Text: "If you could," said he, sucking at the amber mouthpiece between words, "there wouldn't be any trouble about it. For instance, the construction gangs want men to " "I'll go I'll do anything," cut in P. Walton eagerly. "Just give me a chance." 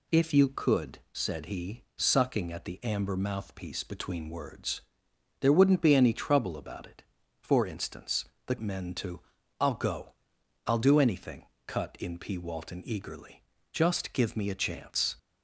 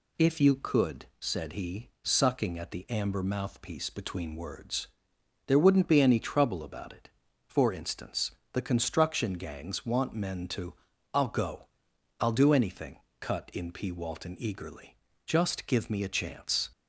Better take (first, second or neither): second